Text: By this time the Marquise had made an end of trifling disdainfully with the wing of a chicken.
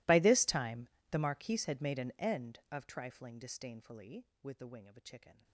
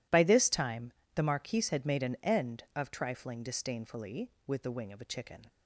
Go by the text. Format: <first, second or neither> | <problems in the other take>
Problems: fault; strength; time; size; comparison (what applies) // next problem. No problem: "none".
second | gets quieter; strong; throughout; 27.5 dB // pauses between "time" and "the"; slight; at 0.8 s; 0.22 s long; slight in the second